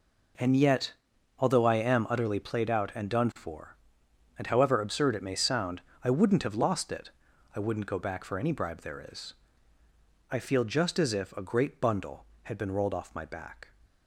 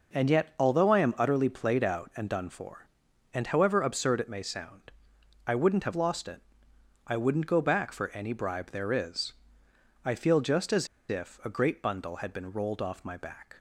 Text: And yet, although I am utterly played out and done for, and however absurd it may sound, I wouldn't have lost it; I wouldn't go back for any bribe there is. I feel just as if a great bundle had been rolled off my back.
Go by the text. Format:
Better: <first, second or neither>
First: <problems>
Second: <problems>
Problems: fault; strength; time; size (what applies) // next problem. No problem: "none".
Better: first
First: none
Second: pauses between "as" and "if"; slight; at 10.8 s; 0.23 s long